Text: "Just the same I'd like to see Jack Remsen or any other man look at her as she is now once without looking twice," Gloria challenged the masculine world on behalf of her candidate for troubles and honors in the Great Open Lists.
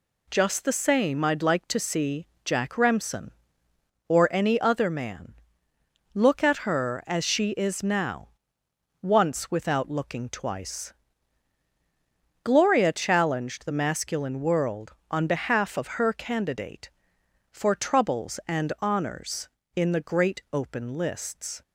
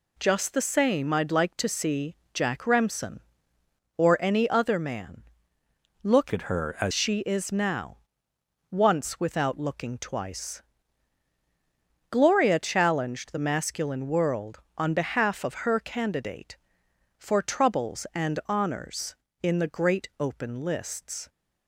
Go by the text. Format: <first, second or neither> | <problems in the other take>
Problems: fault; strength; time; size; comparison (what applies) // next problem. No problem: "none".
first | pauses between "see" and "Jack"; slight; at 2.1 s; 0.18 s long; slight in the first // pauses between "man" and "look"; noticeable; at 5.2 s; 0.80 s long; noticeable in the first // changes voice from "at" to "as"; from 6.3 to 6.9 s; 0.6 s long // pauses between "now" and "once"; noticeable; at 7.9 s; 0.74 s long; noticeable in the first